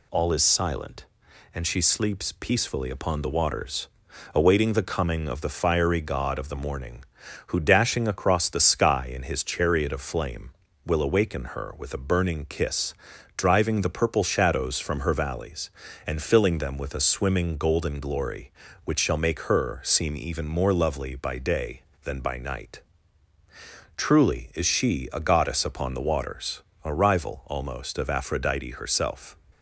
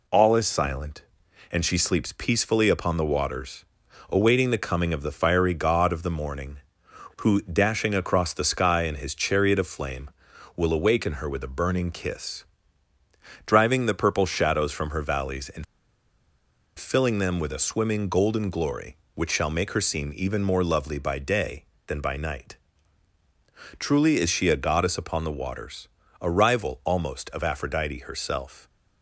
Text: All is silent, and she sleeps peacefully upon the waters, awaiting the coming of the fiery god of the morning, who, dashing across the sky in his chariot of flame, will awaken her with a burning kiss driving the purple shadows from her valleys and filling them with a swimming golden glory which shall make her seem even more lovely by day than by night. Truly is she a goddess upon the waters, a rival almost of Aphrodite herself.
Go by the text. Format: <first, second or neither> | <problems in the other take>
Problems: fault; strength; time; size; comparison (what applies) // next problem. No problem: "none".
first | pauses between "kiss" and "driving"; at 12.4 s; 1.0 s long; also in the first // pauses between "and" and "filling"; at 15.6 s; 1.1 s long